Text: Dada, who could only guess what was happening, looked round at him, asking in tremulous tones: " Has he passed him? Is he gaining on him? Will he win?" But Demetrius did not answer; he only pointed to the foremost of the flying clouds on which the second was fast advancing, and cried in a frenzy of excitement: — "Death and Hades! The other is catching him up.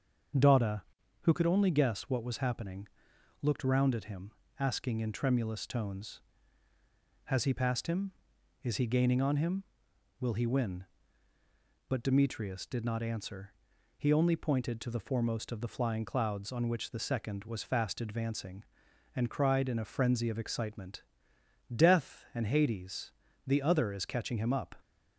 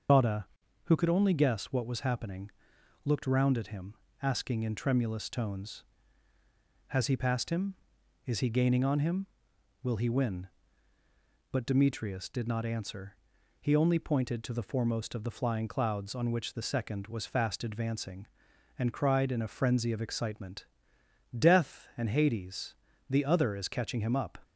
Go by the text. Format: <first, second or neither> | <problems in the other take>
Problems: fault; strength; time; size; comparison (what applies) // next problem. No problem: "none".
first | loses the start of "Dada"; at 0.0 s; 135 ms // starts louder than the rest; until 1.5 s; 6.5 dB; also in the first